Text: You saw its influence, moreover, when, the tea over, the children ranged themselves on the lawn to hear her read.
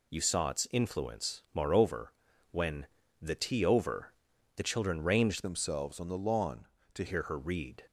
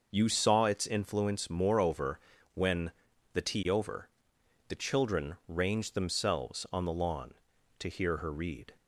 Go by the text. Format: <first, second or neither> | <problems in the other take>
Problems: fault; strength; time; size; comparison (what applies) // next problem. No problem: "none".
second | changes voice from "themselves" to "to"; from 5.4 to 7.0 s; 1.6 s long